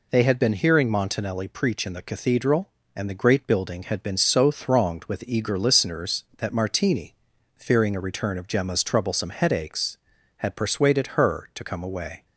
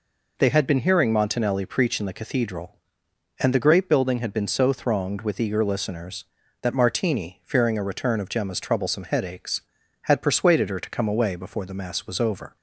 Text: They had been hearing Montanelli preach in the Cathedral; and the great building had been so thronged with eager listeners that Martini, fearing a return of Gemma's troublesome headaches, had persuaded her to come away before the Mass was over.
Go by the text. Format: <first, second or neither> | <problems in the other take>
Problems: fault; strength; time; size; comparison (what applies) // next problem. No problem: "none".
second | stops before "before the Mass was over"; at 12.2 s